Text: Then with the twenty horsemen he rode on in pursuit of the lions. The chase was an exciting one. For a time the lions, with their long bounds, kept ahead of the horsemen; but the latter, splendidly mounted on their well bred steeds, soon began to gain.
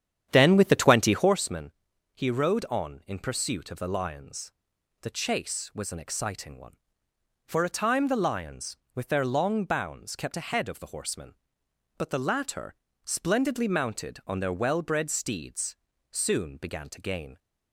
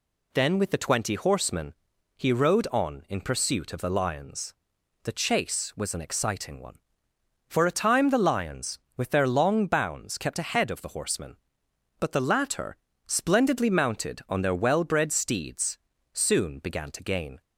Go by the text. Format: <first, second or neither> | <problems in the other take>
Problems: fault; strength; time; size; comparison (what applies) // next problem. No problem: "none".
second | starts louder than the rest; strong; until 1.4 s; 9.5 dB // pauses between "horsemen" and "he"; at 1.7 s; 0.42 s long; also in the second